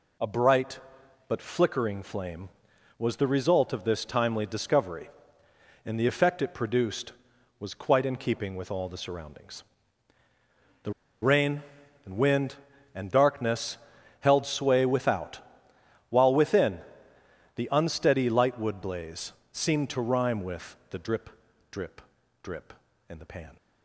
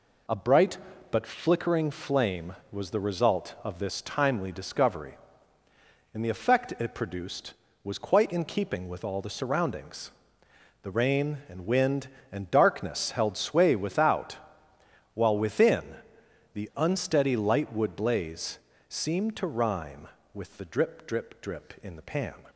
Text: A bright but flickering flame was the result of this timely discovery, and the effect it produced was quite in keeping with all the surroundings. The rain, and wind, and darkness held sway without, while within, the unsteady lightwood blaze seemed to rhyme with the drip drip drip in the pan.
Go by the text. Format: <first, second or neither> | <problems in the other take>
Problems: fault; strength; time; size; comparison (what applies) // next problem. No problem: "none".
second | pauses between "The" and "rain"; slight; at 10.9 s; 0.29 s long // pauses between "darkness" and "held"; at 13.7 s; 0.42 s long // pauses between "blaze" and "seemed"; slight; at 19.3 s; 0.20 s long; slight in the second // pauses between "drip" and "drip"; at 21.2 s; 0.40 s long // pauses between "drip" and "drip"; at 22.0 s; 0.40 s long